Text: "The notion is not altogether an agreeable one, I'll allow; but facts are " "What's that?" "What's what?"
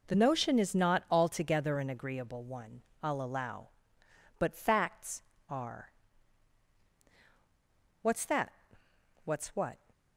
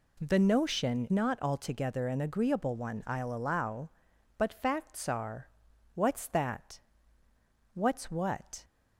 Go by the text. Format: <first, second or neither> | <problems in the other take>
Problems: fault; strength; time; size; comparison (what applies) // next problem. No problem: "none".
first | skips "is"; at 1.0 s